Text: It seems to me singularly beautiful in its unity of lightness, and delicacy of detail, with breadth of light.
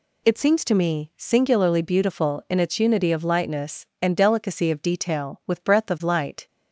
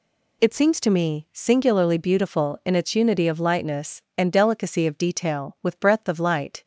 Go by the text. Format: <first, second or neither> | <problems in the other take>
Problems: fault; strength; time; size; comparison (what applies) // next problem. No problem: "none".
neither | none